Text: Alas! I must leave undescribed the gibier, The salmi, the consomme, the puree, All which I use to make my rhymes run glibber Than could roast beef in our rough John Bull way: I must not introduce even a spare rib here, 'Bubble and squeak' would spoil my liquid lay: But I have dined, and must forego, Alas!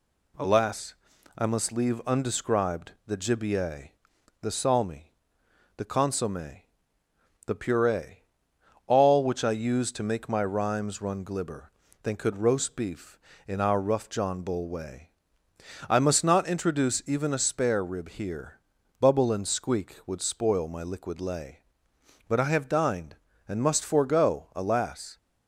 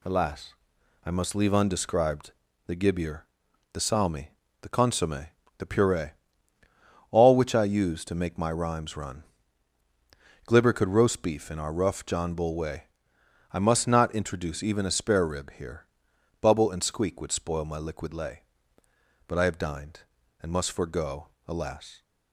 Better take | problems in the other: first | pauses between "undescribed" and "the"; slight; at 2.3 s; 0.34 s long; slight in the first // pauses between "run" and "glibber"; at 9.2 s; 1.2 s long // skips "Than"; at 10.7 s

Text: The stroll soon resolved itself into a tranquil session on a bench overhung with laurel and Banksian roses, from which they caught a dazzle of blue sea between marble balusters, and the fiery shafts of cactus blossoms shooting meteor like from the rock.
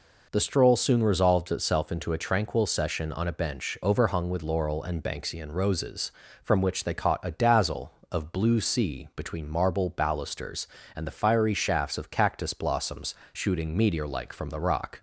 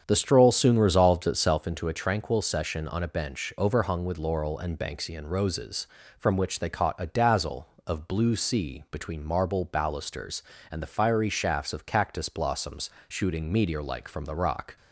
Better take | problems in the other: first | starts louder than the rest; strong; until 1.8 s; 7.5 dB // pauses between "blossoms" and "shooting"; slight; at 12.8 s; 0.18 s long; slight in the first

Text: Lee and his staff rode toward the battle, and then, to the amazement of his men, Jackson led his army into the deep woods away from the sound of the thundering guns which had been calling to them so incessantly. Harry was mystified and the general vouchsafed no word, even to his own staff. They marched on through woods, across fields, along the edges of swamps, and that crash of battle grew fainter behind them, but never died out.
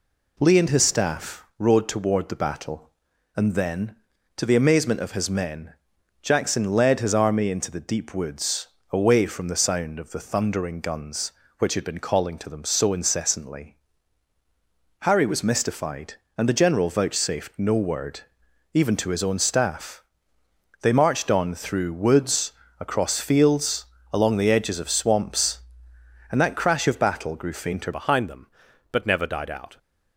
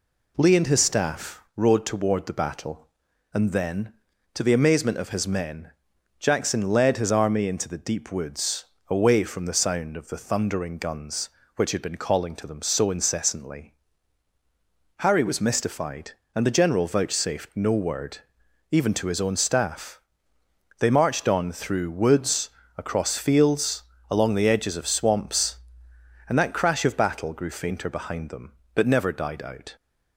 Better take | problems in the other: second | pauses between "woods" and "away"; slight; at 8.6 s; 0.24 s long; slight in the second // changes voice at "behind"; from 27.9 s on; 1.8 s long

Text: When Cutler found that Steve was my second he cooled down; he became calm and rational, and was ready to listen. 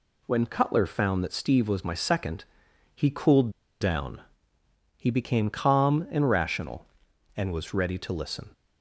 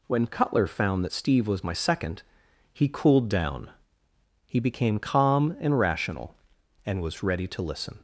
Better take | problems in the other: second | pauses between "second" and "he"; noticeable; at 2.4 s; 0.50 s long; noticeable in the second // pauses between "cooled" and "down"; slight; at 3.5 s; 0.30 s long

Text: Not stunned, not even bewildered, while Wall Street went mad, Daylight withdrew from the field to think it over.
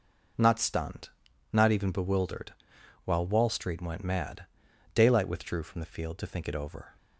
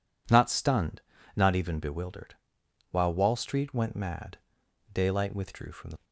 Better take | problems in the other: first | stops before "field to think it over"; at 6.0 s

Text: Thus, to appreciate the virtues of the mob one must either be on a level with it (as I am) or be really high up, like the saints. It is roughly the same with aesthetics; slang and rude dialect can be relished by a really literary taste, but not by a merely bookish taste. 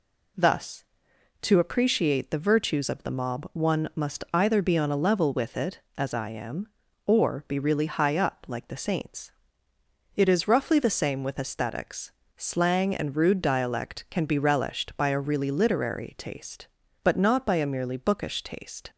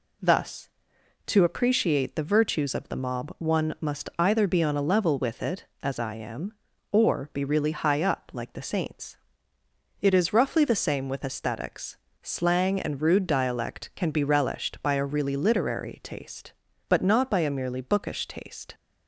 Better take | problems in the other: neither | none

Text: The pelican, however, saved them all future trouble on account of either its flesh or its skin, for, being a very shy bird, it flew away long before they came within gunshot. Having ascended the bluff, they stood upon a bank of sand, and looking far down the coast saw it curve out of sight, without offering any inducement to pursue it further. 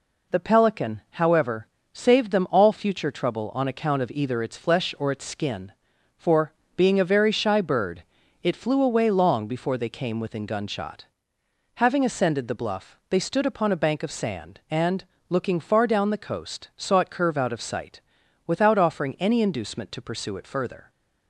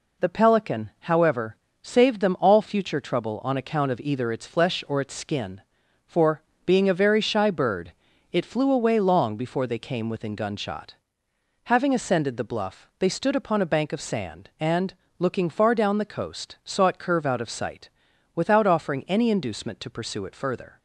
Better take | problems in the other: neither | pauses between "and" and "looking"; slight; the same in both

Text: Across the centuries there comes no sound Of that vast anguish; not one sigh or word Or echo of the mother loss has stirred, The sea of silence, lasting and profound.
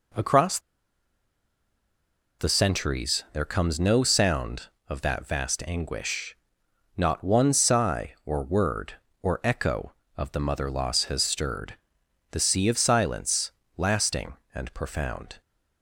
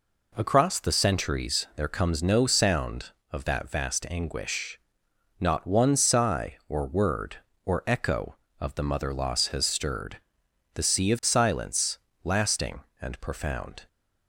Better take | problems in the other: second | pauses between "Across" and "the"; strong; at 0.5 s; 1.8 s long

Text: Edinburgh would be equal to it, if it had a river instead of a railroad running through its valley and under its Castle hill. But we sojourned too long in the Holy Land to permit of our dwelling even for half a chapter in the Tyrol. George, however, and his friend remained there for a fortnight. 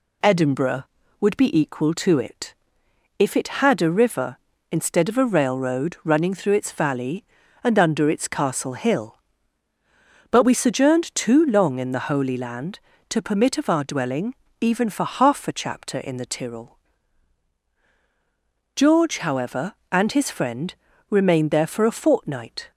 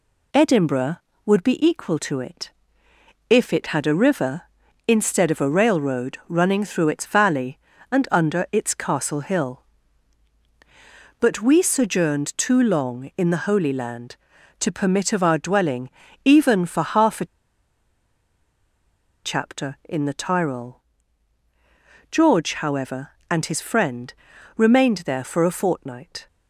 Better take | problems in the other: first | pauses between "dwelling" and "even"; slight; at 15.8 s; 0.34 s long; slight in the first // pauses between "a" and "chapter"; strong; at 17.2 s; 1.9 s long // pauses between "friend" and "remained"; at 24.1 s; 0.42 s long; slight in the first

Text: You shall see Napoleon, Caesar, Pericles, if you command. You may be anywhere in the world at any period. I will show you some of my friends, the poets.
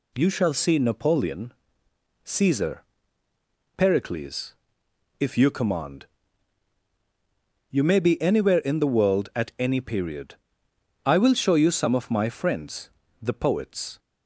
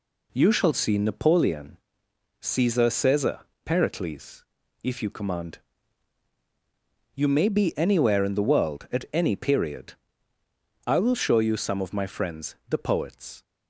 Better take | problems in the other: first | says "Caesar" twice; at 2.8 s

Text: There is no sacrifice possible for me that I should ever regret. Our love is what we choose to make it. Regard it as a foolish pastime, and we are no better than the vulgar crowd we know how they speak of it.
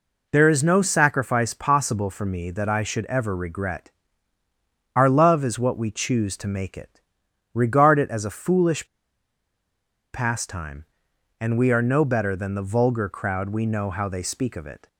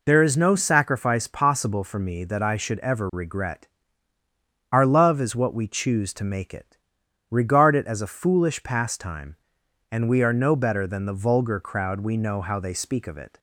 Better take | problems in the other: second | pauses between "foolish" and "pastime"; strong; at 8.8 s; 1.2 s long

